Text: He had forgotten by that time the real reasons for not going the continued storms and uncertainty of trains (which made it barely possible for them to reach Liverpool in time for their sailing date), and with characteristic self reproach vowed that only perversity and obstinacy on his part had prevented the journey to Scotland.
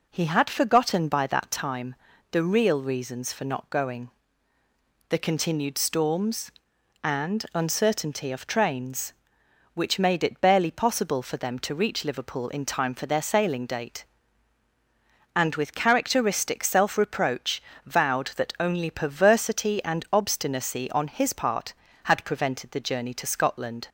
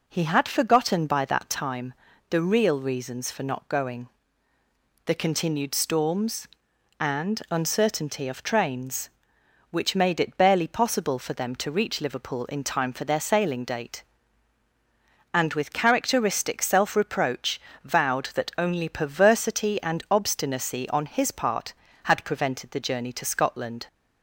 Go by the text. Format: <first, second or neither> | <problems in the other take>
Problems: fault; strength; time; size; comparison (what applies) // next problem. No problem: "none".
neither | pauses between "time" and "the"; slight; the same in both // pauses between "going" and "the"; noticeable; the same in both // pauses between "reproach" and "vowed"; slight; the same in both